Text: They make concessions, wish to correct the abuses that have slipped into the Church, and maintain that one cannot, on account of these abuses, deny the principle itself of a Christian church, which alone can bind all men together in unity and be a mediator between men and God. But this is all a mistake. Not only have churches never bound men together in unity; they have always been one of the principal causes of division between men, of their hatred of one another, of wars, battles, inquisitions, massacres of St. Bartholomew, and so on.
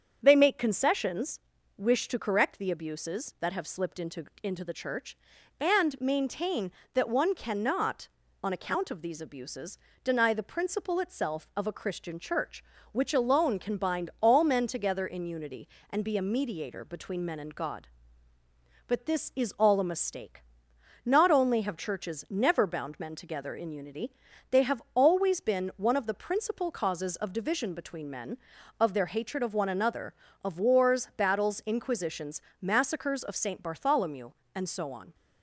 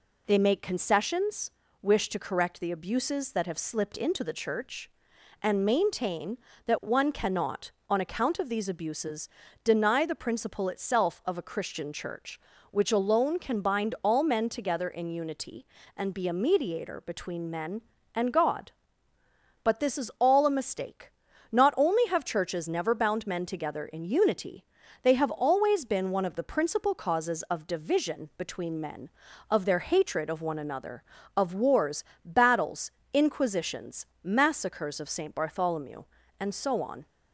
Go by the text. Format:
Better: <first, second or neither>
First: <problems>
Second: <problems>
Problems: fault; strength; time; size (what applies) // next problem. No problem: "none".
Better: second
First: starts louder than the rest; strong; until 1.2 s; 7 dB // says "into" twice; at 4.4 s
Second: none